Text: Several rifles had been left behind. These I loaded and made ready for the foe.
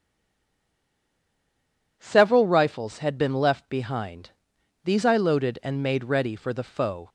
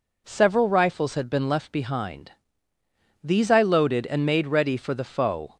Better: second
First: stays silent before the first word; noticeable; until 1.9 s; 1.9 s long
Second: none

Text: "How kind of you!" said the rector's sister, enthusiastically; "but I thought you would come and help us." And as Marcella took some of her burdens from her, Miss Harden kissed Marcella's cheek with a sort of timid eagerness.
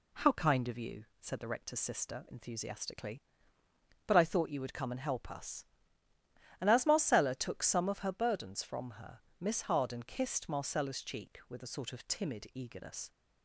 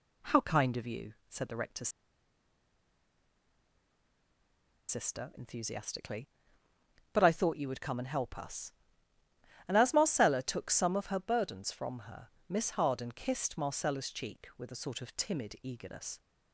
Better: first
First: none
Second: pauses between "rector's" and "sister"; strong; at 1.8 s; 2.9 s long

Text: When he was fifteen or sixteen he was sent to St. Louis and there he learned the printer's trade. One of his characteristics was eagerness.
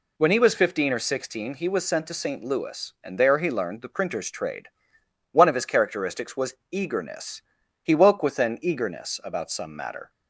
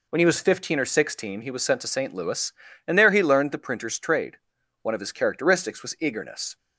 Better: second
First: pauses between "was" and "eagerness"; slight; at 6.5 s; 0.16 s long // goes on to say "He woke with an eagerness about some matter"; strong; from 7.8 s on; 2.2 s long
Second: none

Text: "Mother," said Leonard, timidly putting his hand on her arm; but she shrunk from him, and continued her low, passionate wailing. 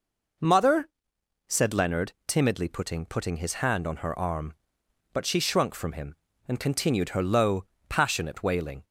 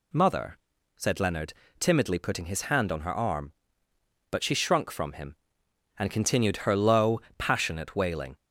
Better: second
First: says "putting" twice; at 3.0 s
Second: none

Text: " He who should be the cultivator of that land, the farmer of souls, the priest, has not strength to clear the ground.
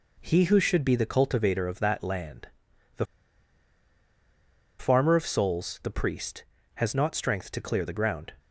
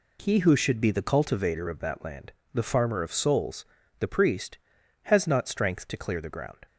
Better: second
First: pauses between "the" and "farmer"; strong; at 3.0 s; 1.7 s long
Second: none

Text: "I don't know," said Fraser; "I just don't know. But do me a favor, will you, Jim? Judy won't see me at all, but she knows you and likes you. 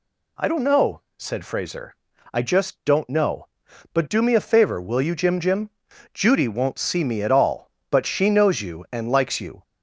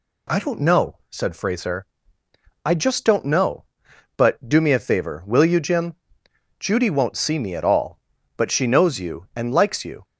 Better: second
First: says "Jim" twice; at 5.3 s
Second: none

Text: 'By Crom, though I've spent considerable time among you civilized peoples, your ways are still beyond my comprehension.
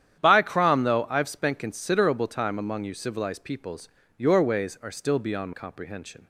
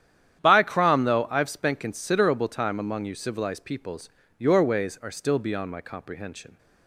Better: second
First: starts louder than the rest; strong; until 1.2 s; 10 dB // skips "my"; at 5.5 s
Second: starts louder than the rest; strong; until 1.4 s; 10 dB

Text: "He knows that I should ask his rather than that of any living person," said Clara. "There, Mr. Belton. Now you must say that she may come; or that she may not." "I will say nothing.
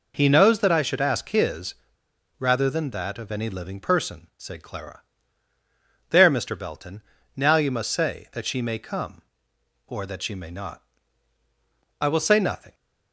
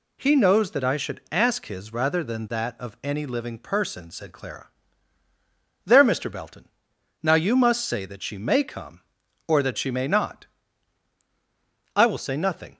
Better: second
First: pauses between "his" and "rather"; noticeable; at 1.7 s; 0.64 s long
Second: none

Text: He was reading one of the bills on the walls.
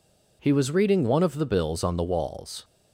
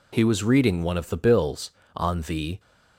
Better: first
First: none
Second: stops before "walls"; at 2.5 s

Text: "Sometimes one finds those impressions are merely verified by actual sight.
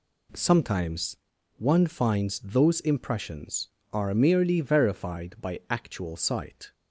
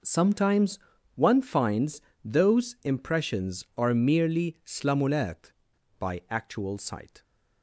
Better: first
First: pauses between "Sometimes" and "one"; at 1.1 s; 0.42 s long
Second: pauses between "Sometimes" and "one"; at 0.7 s; 0.38 s long // pauses between "finds" and "those"; slight; at 1.9 s; 0.24 s long // says "slamulat" for "verified"; at 4.6 s

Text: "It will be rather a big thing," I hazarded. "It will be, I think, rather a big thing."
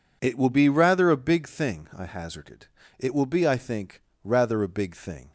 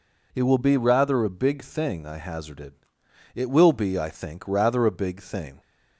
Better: neither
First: none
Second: none

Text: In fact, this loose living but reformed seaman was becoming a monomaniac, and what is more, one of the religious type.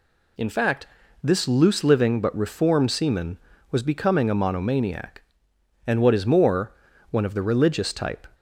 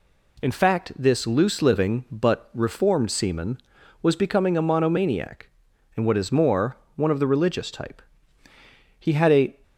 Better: first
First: none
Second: goes on to say "He had a"; from 8.9 s on; 0.60 s long

